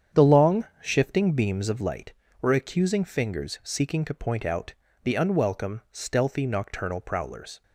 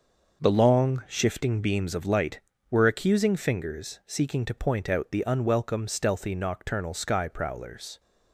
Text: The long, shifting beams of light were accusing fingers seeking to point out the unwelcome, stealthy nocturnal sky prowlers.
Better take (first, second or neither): second